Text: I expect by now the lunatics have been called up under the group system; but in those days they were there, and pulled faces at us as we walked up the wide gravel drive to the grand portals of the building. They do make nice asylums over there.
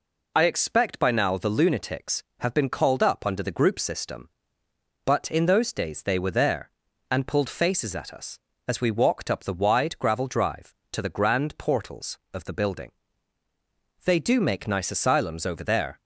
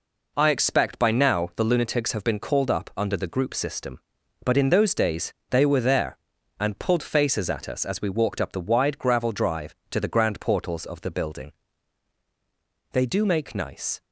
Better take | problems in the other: first | pauses between "days" and "they"; slight; at 5.3 s; 0.16 s long // stops before "asylums over there"; at 14.0 s

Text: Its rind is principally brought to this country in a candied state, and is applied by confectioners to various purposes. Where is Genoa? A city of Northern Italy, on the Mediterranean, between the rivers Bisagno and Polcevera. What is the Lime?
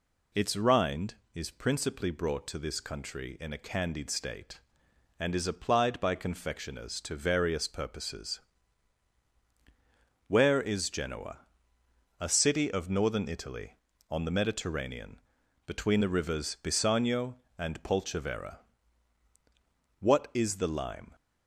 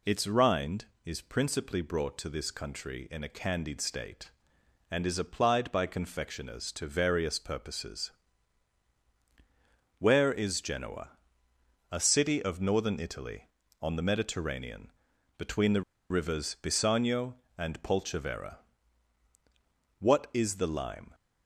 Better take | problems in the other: first | pauses between "the" and "rivers"; slight; at 15.8 s; 0.29 s long

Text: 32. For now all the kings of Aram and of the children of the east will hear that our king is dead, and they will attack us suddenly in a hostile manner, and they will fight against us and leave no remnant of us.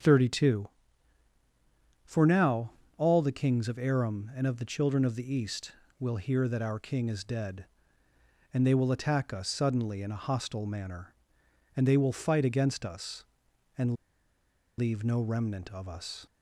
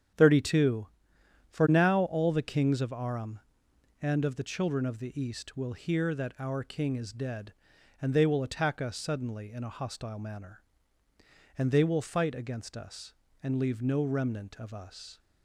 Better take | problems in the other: second | starts louder than the rest; strong; until 2.4 s; 7 dB; strong in the second // pauses between "now" and "all"; slight; at 2.7 s; 0.26 s long // pauses between "and" and "leave"; noticeable; at 13.9 s; 0.84 s long

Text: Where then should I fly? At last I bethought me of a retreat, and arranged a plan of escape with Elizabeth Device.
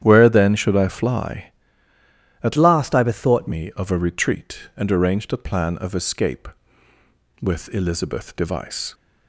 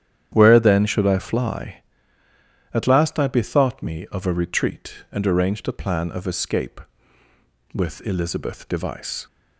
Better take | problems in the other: second | starts louder than the rest; strong; until 1.0 s; 10 dB; strong in the second // changes voice from "last" to "bethought"; from 2.5 to 3.4 s; 0.9 s long

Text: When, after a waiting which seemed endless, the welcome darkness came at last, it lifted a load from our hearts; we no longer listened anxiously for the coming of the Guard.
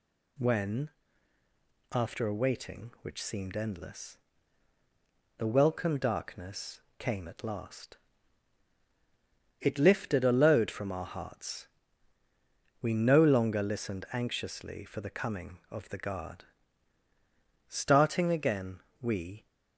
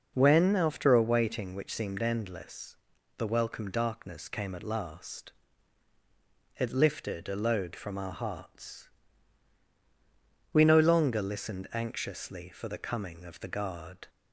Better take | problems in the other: second | pauses between "darkness" and "came"; slight; at 6.8 s; 0.16 s long // goes on to say "Starting again we"; strong; from 17.6 s on; 1.8 s long

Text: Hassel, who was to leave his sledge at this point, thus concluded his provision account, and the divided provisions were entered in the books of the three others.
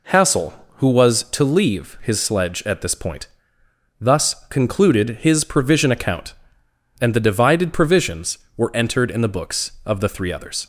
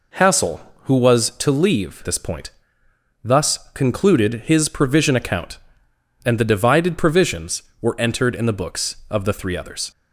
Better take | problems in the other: first | skips "his sledge at"; at 2.0 s // pauses between "thus" and "concluded"; slight; at 3.5 s; 0.16 s long

